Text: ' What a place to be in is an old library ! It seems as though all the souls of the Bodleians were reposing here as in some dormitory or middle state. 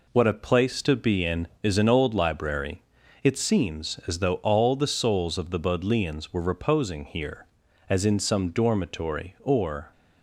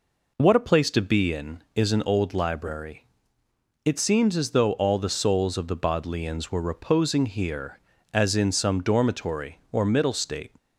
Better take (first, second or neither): second